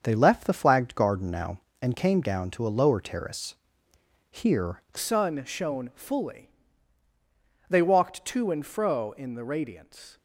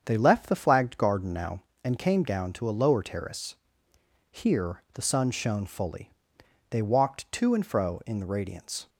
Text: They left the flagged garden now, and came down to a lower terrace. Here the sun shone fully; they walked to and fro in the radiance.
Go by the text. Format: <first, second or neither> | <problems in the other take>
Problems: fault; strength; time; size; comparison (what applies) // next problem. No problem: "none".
second | starts louder than the rest; until 1.0 s; 6.5 dB; strong in the second // changes voice at "sun"; from 4.9 s on; 5.2 s long